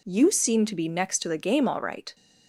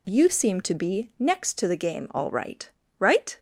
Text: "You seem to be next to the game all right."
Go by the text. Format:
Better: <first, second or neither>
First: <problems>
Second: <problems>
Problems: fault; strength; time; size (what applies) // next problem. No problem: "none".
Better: first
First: none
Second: says "right" twice; at 2.9 s